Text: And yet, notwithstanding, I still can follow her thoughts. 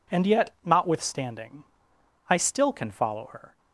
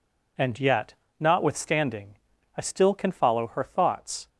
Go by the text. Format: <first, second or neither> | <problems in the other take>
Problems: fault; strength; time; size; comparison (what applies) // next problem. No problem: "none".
second | stops before "thoughts"; at 3.5 s